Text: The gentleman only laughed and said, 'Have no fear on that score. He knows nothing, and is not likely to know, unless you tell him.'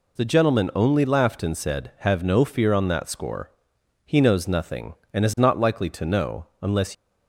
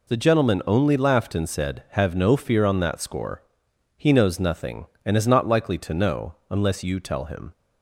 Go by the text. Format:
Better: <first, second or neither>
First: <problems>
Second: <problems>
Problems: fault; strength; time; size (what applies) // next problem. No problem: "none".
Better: second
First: stops before "you tell him"; at 6.9 s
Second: none